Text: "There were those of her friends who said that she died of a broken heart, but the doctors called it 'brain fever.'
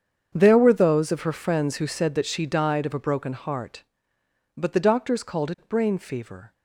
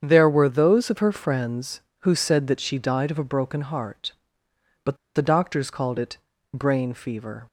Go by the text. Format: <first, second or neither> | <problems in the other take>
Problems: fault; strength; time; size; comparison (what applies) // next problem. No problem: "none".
first | starts louder than the rest; strong; until 1.0 s; 7.5 dB; strong in the first // pauses between "but" and "the"; slight; at 4.9 s; 0.20 s long // pauses between "it" and "brain"; at 6.1 s; 0.38 s long